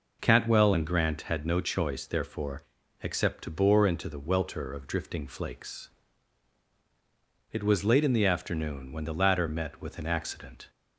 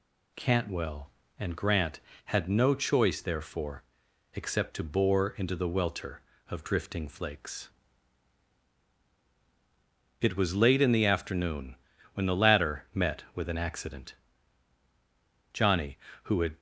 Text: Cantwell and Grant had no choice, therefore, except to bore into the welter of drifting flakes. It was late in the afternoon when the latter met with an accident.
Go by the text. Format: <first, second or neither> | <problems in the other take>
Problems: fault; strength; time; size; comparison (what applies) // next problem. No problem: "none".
first | pauses between "afternoon" and "when"; at 11.7 s; 0.38 s long // goes on to say "Johnny who had"; noticeable; from 15.5 s on; 1.0 s long